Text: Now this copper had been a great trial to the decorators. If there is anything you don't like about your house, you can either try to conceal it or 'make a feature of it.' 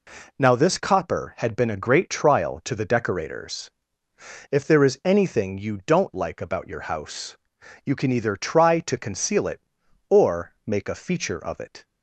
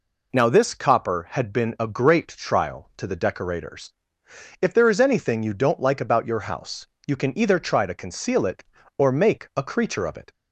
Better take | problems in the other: first | says "creature" for "feature"; at 9.6 s

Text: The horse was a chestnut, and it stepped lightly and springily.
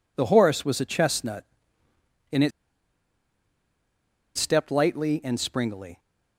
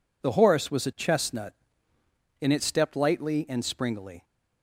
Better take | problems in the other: second | pauses between "it" and "stepped"; strong; at 2.5 s; 1.8 s long

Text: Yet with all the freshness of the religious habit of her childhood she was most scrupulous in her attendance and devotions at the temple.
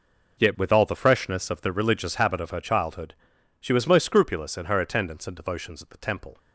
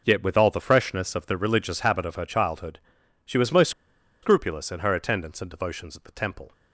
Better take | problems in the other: first | pauses between "childhood" and "she"; noticeable; at 2.7 s; 0.48 s long; noticeable in the first // pauses between "most" and "scrupulous"; noticeable; at 3.7 s; 0.52 s long

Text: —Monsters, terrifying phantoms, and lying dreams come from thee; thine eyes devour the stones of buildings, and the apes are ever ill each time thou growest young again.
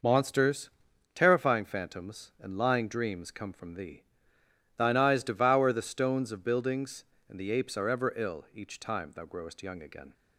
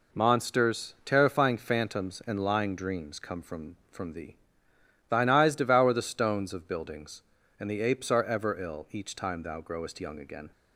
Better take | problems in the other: first | says "from" twice; at 3.8 s

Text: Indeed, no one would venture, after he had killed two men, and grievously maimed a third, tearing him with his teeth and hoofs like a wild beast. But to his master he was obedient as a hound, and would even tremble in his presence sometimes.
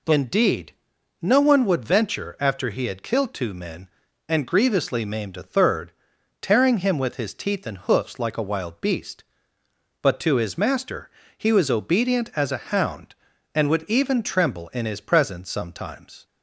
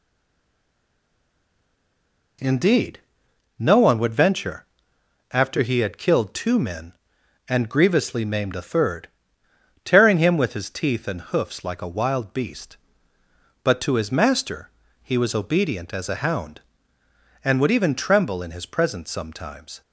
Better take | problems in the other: first | stays silent before the first word; until 2.3 s; 2.3 s long // pauses between "master" and "he"; slight; at 14.6 s; 0.34 s long; slight in the first

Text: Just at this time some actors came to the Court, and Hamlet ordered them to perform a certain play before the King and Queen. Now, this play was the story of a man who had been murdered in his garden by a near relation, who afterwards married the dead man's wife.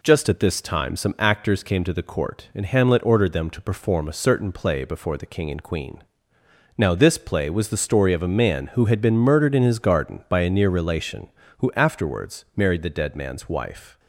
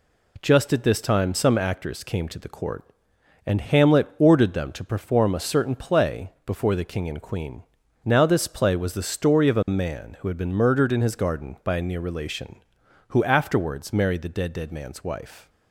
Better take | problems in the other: first | says "dead" twice; at 14.5 s

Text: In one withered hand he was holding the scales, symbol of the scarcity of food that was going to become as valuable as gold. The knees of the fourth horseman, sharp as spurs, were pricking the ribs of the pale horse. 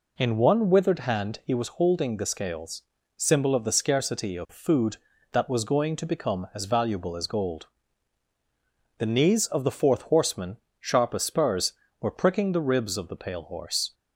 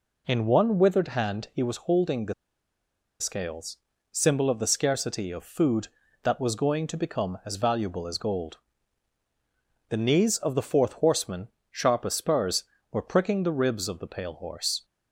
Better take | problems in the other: first | pauses between "the" and "scales"; noticeable; at 2.3 s; 0.86 s long

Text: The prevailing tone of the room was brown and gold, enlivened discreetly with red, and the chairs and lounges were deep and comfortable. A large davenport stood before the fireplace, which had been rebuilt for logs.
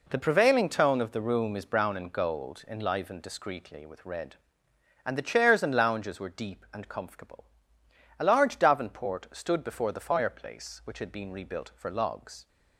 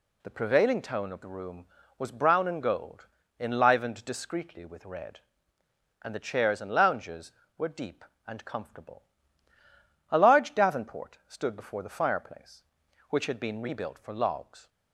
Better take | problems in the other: second | says "is" for "was"; at 1.5 s

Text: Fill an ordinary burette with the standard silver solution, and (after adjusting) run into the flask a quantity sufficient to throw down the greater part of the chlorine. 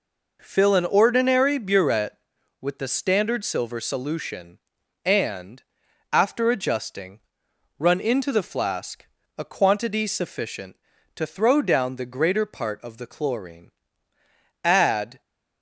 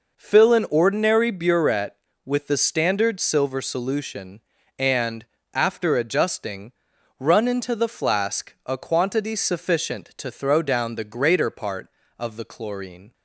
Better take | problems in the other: second | pauses between "flask" and "a"; slight; at 9.0 s; 0.32 s long // goes on to say "Add"; from 14.6 s on; 0.56 s long

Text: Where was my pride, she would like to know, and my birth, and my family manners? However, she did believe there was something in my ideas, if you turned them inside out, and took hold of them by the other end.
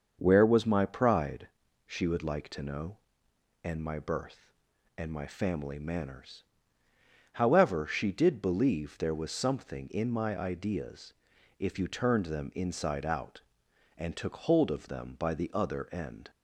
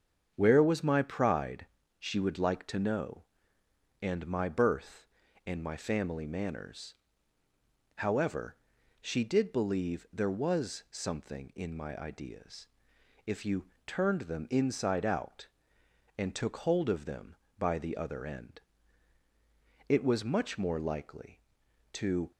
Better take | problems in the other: first | starts louder than the rest; strong; until 1.3 s; 7.5 dB; also in the first // pauses between "you" and "turned"; slight; at 13.6 s; 0.20 s long // goes on to say "It was much more likely to"; strong; from 19.8 s on; 2.4 s long

